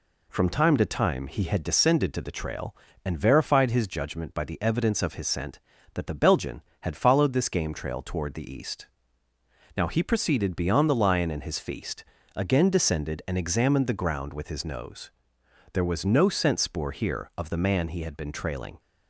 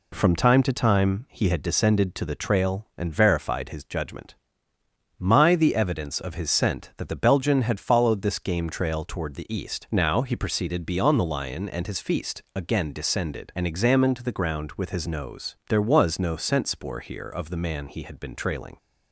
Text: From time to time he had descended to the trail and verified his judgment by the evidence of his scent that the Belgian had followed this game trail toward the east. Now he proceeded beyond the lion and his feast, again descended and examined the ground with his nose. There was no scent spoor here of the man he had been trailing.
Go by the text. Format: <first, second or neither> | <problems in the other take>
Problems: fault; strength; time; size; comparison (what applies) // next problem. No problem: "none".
first | says "my" for "by"; at 5.1 s